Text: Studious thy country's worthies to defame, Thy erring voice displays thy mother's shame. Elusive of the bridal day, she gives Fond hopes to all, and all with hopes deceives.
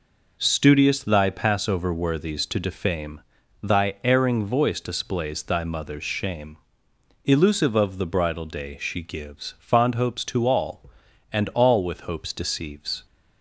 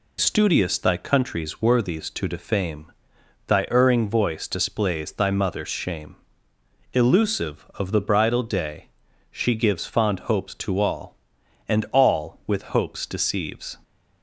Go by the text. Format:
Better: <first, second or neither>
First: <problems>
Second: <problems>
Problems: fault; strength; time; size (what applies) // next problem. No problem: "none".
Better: second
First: says "passover" for "country's"; at 1.2 s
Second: none